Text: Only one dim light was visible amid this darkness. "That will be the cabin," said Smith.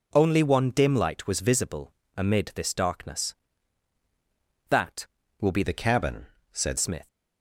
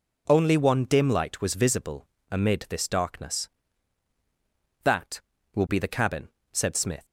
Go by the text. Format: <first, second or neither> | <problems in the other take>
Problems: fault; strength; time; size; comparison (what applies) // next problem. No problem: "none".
second | pauses between "visible" and "amid"; slight; at 1.9 s; 0.24 s long; slight in the second // changes voice from "the" to "said"; from 5.6 to 6.7 s; 1.1 s long